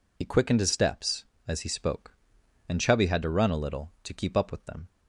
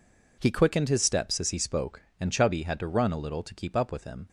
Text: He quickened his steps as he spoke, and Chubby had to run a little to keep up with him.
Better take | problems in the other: second | says "them" for "him"; at 4.6 s

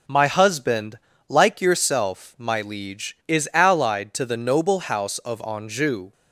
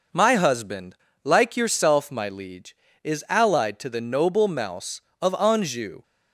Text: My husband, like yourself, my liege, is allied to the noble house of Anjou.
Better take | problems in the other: first | says "mouse" for "house"; at 4.4 s

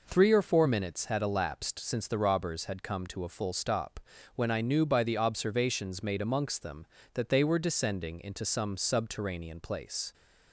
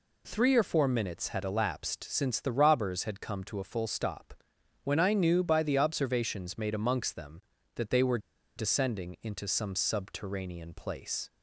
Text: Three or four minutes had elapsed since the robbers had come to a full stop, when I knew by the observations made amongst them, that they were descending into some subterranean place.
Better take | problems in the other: first | pauses between "were" and "descending"; at 8.1 s; 0.38 s long

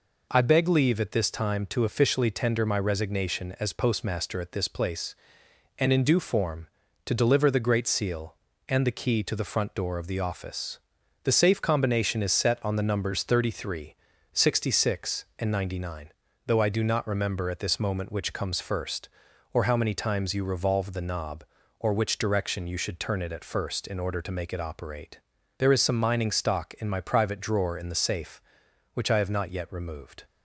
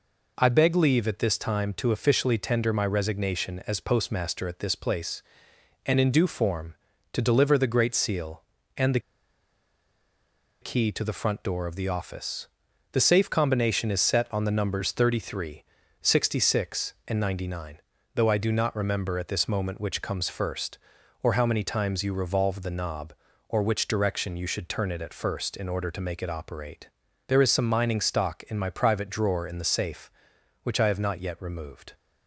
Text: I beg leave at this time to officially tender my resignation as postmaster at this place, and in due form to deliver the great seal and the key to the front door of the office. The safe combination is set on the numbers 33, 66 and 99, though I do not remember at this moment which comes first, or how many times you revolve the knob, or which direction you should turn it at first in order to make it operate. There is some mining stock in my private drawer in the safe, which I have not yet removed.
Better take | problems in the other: first | pauses between "the" and "key"; strong; at 8.9 s; 1.6 s long

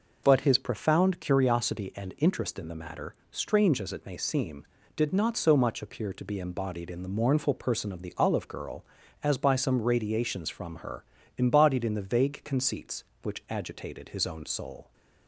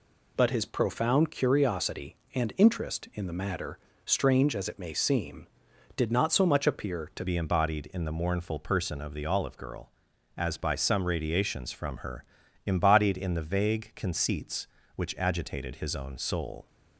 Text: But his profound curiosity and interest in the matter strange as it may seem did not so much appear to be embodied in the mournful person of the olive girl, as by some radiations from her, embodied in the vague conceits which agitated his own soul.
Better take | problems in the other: first | pauses between "matter" and "strange"; slight; at 3.7 s; 0.26 s long; slight in the first // changes voice at "be"; from 7.2 s on; 9.4 s long

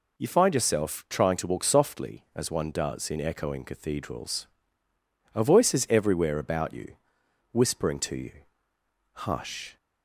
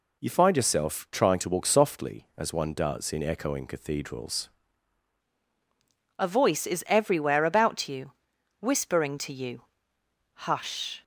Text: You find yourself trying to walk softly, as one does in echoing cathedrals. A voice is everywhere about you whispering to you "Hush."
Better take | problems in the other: first | changes voice at "A"; from 6.1 s on; 4.9 s long // pauses between "you" and "whispering"; noticeable; at 8.1 s; 0.48 s long; noticeable in the first // pauses between "you" and "Hush"; noticeable; at 9.6 s; 0.86 s long; noticeable in the first

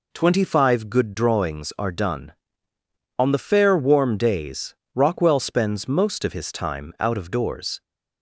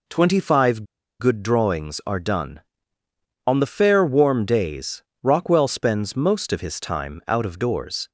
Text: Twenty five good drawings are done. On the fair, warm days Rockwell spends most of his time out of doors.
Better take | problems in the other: first | pauses between "five" and "good"; slight; at 0.8 s; 0.35 s long // pauses between "days" and "Rockwell"; slight; at 5.0 s; 0.20 s long; slight in the first

